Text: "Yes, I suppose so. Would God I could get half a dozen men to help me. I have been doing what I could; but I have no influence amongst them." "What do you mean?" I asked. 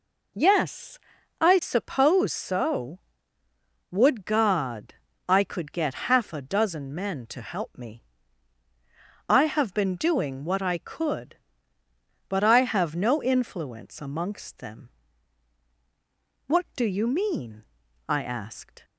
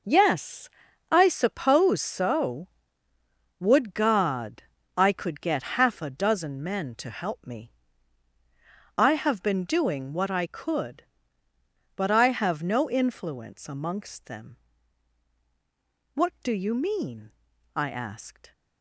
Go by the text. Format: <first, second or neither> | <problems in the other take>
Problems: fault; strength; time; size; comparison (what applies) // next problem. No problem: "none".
first | gets quieter; strong; throughout; 9.5 dB // pauses between "God" and "I"; slight; at 4.6 s; 0.32 s long; slight in the first